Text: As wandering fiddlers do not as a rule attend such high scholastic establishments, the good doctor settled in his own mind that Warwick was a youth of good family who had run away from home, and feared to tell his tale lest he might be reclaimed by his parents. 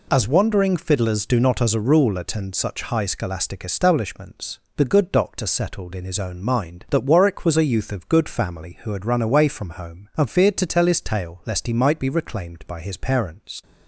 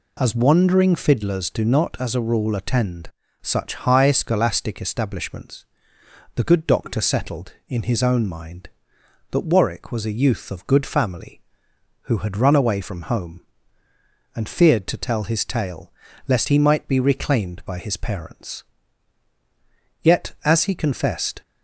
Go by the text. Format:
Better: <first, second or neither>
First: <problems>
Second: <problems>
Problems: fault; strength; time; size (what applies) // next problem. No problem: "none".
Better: first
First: none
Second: pauses between "attend" and "such"; slight; at 3.1 s; 0.30 s long // pauses between "tale" and "lest"; slight; at 15.9 s; 0.36 s long // goes on to say "Yet as he confessed"; from 20.0 s on; 1.4 s long